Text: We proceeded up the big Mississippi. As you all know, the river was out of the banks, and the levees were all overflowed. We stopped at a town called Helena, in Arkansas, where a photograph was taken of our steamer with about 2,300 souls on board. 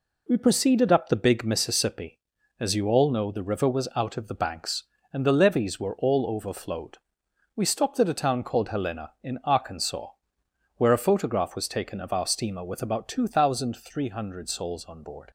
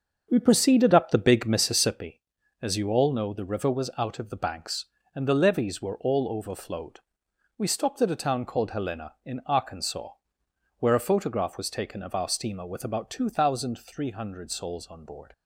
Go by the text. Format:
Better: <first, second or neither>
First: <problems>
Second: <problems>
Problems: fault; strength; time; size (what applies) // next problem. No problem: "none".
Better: first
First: none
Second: starts louder than the rest; until 2.1 s; 7 dB